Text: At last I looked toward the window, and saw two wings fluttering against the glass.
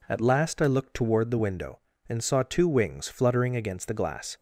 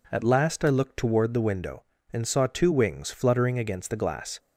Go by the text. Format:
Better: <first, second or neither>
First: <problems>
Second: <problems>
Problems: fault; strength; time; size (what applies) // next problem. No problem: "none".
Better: neither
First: none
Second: none